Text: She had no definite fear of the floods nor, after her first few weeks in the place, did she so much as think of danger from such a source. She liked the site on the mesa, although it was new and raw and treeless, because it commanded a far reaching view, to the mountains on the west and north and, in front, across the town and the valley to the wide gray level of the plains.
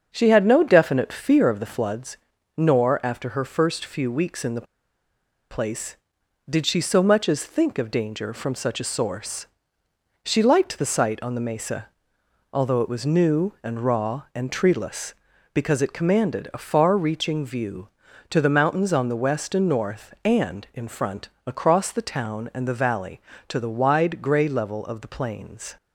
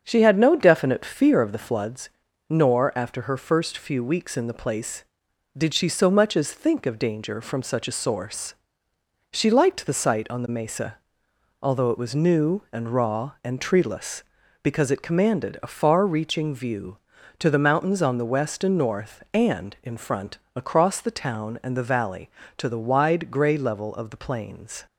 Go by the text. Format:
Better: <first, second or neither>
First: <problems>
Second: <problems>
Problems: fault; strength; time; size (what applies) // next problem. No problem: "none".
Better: second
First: starts louder than the rest; until 1.1 s; 7 dB // pauses between "floods" and "nor"; slight; at 2.1 s; 0.36 s long // pauses between "the" and "place"; noticeable; at 4.6 s; 0.86 s long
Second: starts louder than the rest; until 1.0 s; 7 dB // pauses between "floods" and "nor"; slight; at 2.1 s; 0.36 s long